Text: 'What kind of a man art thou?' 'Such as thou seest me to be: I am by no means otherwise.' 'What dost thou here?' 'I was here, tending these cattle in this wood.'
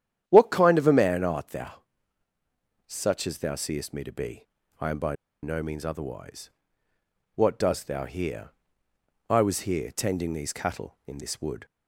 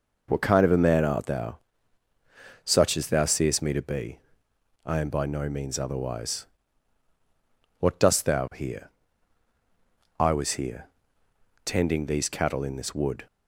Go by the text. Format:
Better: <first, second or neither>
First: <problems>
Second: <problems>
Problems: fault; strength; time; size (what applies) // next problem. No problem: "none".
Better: second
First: starts louder than the rest; strong; until 1.2 s; 10.5 dB // pauses between "by" and "no"; slight; at 5.1 s; 0.28 s long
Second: none